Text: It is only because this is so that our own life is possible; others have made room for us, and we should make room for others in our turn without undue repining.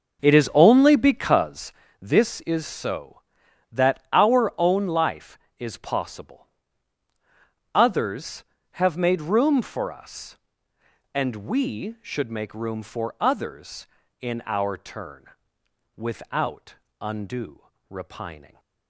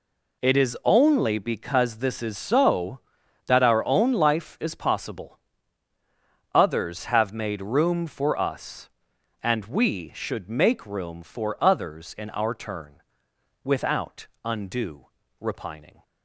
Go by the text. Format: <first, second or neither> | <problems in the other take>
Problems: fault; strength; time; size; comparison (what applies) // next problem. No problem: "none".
second | starts louder than the rest; noticeable; until 1.6 s; 6 dB // pauses between "because" and "this"; slight; at 1.7 s; 0.30 s long // pauses between "turn" and "without"; noticeable; at 15.2 s; 0.70 s long; noticeable in the second // pauses between "without" and "undue"; slight; at 16.7 s; 0.24 s long; slight in the second // pauses between "undue" and "repining"; slight; at 17.6 s; 0.28 s long; slight in the second